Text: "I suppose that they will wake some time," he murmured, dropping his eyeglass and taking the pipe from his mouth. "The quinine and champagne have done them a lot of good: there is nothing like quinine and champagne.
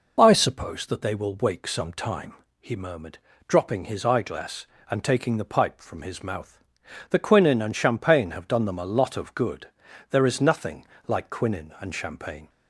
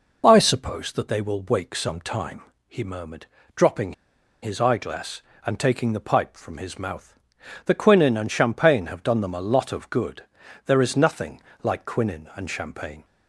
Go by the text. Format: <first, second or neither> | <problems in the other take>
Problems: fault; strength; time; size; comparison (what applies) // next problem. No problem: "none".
first | pauses between "dropping" and "his"; noticeable; at 3.9 s; 0.49 s long // pauses between "nothing" and "like"; slight; at 11.4 s; 0.20 s long; slight in the first